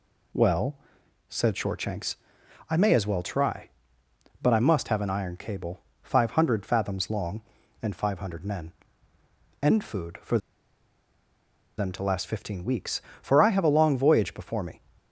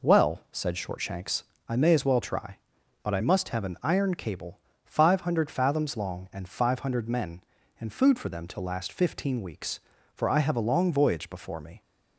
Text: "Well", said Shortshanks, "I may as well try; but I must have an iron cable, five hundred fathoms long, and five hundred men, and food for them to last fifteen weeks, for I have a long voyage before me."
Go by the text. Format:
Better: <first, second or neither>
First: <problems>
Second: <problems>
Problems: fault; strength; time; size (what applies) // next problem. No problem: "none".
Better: second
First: pauses between "for" and "them"; strong; at 10.3 s; 1.3 s long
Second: none